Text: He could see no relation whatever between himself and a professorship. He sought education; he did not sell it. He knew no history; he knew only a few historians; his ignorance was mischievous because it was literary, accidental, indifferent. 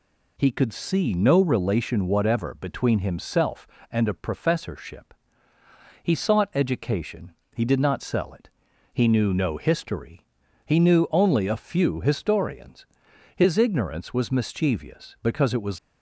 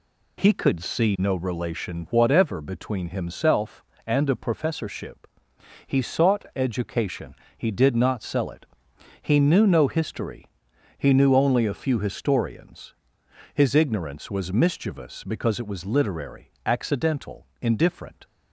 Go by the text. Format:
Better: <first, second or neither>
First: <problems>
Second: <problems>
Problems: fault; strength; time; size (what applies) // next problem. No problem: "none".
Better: second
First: stops before "literary accidental indifferent"; at 15.7 s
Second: none